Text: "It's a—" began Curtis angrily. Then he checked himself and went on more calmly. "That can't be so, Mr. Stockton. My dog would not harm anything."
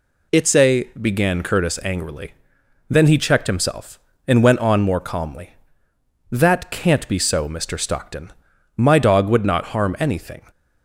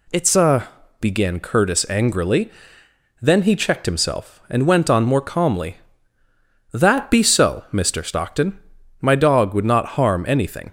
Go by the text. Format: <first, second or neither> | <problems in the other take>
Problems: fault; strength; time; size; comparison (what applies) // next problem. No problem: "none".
first | skips "can't"; at 7.1 s